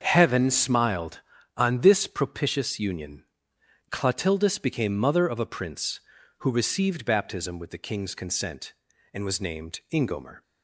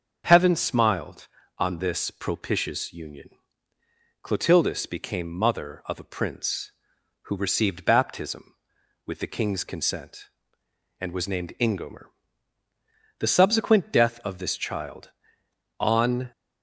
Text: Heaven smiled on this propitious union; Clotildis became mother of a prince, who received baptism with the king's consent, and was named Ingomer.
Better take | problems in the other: first | starts louder than the rest; until 1.2 s; 6.5 dB; also in the first // goes on to say "The subsequent death of this child on"; strong; from 13.1 s on; 3.1 s long

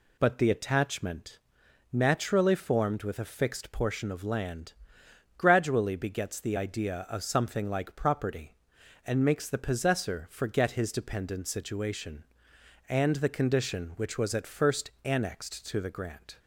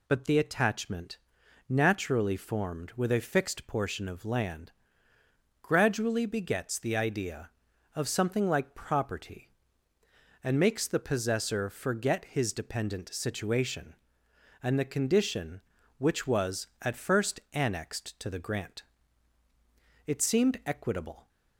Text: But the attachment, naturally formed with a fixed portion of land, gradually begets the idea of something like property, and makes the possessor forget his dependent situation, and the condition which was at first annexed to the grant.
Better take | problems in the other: first | goes on to say "It seemed equitable"; noticeable; from 20.0 s on; 1.2 s long

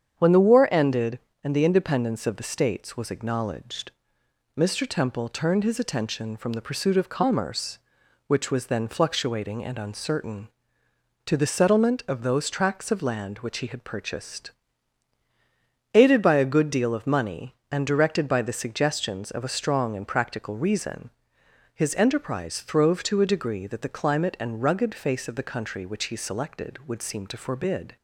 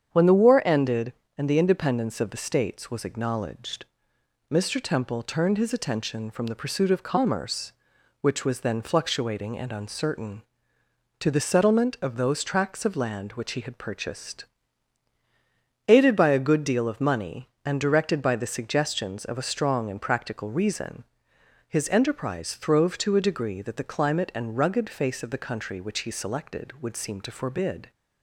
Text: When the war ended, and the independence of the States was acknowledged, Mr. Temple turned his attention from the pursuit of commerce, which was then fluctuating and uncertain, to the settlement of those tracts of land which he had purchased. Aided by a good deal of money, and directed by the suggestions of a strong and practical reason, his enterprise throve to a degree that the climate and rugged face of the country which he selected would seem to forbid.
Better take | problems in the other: neither | starts louder than the rest; strong; the same in both

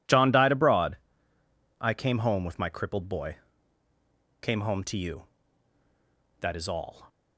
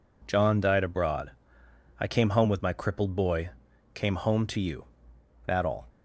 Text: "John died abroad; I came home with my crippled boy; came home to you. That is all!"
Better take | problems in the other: first | skips "is"; at 5.6 s

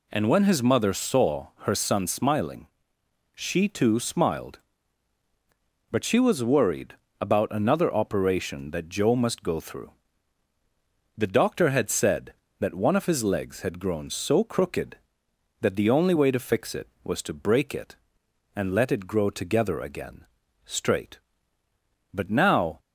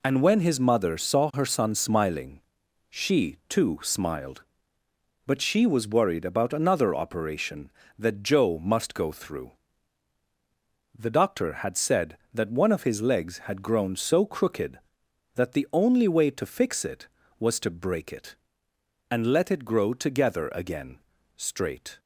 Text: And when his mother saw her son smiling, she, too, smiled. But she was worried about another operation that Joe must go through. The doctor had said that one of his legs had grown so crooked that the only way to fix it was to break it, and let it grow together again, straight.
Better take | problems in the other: second | pauses between "saw" and "her"; slight; at 1.4 s; 0.16 s long // pauses between "worried" and "about"; slight; at 6.9 s; 0.26 s long // goes on to say "But now"; noticeable; from 22.1 s on; 0.66 s long

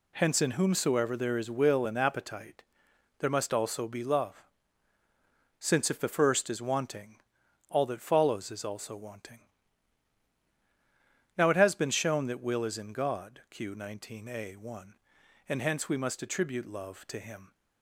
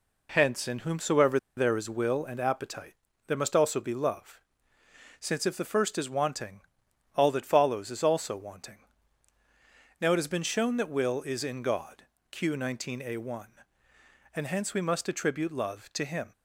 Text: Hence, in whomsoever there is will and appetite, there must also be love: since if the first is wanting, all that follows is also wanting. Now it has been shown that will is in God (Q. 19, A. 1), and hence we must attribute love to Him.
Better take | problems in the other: first | pauses between "whomsoever" and "there"; slight; at 1.3 s; 0.18 s long

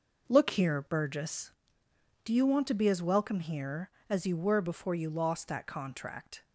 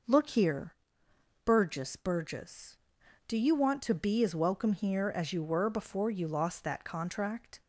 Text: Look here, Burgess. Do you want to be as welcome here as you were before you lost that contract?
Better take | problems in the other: first | says "Burgess" twice; at 1.9 s

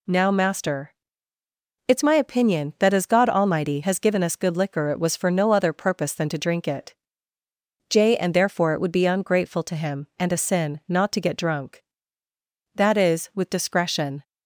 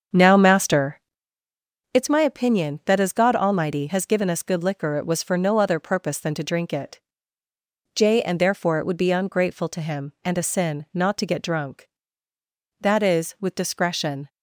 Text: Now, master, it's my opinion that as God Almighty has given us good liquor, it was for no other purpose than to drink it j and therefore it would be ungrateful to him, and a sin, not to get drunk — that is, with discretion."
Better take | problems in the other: first | starts louder than the rest; strong; until 1.6 s; 7 dB // pauses between "it" and "j"; noticeable; at 6.9 s; 0.98 s long; noticeable in the first

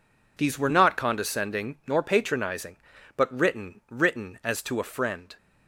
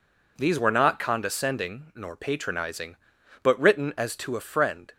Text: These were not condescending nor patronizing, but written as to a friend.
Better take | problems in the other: second | says "written" twice; at 3.8 s

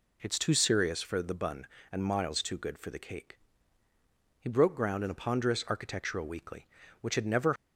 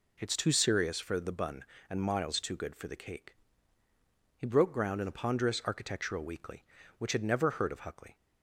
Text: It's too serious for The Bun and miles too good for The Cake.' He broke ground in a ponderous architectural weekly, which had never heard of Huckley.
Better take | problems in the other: second | stops before "heard of Huckley"; at 7.5 s

